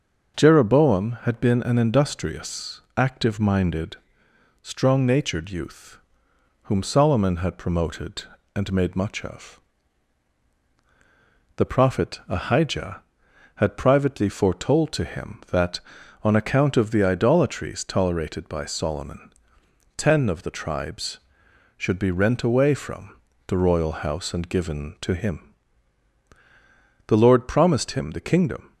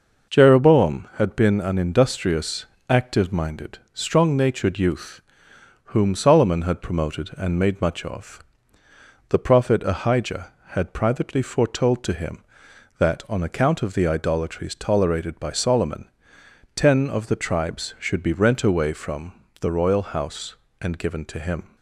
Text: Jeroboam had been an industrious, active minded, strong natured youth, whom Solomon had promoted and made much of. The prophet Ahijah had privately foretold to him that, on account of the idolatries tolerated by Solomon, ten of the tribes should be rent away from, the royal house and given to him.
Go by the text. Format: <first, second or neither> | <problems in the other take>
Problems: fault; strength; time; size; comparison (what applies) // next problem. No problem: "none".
second | starts louder than the rest; until 1.4 s; 6 dB // goes on to say "The Lord promised him the kingdom"; from 27.0 s on; 1.6 s long